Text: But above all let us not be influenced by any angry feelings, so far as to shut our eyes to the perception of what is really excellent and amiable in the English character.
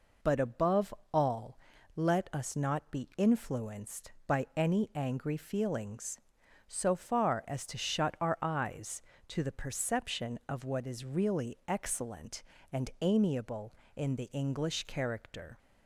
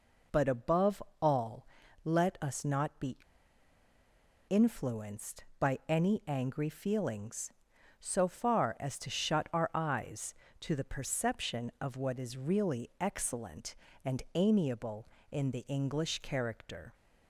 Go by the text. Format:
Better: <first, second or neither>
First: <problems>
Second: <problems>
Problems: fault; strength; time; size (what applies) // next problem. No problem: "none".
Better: first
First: pauses between "above" and "all"; slight; at 0.9 s; 0.20 s long // pauses between "all" and "let"; at 1.5 s; 0.40 s long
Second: pauses between "above" and "all"; slight; at 1.0 s; 0.20 s long // pauses between "all" and "let"; at 1.6 s; 0.40 s long // pauses between "be" and "influenced"; strong; at 3.1 s; 1.3 s long